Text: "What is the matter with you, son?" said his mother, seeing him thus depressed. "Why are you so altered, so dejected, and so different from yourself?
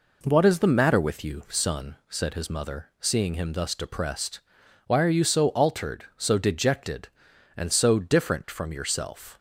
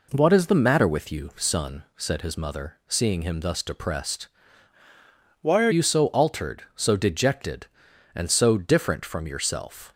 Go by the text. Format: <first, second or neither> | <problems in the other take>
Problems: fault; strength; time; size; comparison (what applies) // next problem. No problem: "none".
first | changes voice from "Why" to "are"; from 5.4 to 5.6 s; 0.2 s long